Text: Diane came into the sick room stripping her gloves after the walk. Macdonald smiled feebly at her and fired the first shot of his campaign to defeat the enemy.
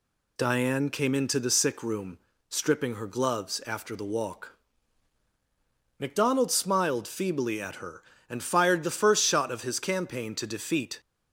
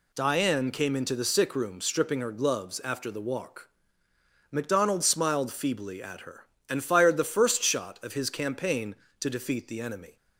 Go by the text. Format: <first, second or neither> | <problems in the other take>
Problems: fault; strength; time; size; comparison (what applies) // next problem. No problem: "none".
second | pauses between "room" and "stripping"; slight; at 2.1 s; 0.30 s long // stops before "the enemy"; at 10.9 s